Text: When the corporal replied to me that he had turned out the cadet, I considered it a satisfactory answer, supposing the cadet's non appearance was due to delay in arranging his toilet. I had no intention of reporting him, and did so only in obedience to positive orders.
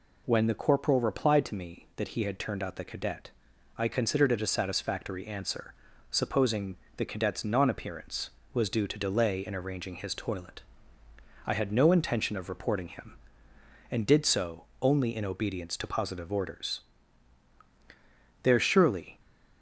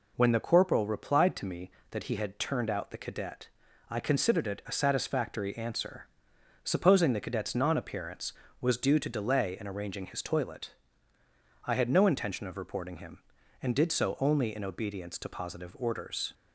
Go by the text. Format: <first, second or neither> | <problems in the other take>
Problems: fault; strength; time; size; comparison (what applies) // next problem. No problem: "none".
second | pauses between "supposing" and "the"; slight; at 6.7 s; 0.20 s long // pauses between "so" and "only"; slight; at 14.6 s; 0.18 s long // goes on to say "There surely"; noticeable; from 18.4 s on; 0.76 s long